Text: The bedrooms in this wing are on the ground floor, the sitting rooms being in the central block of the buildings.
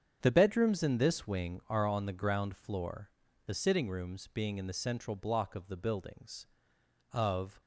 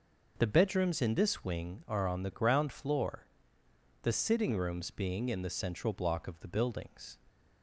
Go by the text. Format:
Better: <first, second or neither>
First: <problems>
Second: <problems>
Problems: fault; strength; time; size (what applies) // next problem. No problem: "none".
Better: second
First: starts louder than the rest; strong; until 1.2 s; 8 dB // goes on to say "Of"; slight; from 7.1 s on; 0.48 s long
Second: none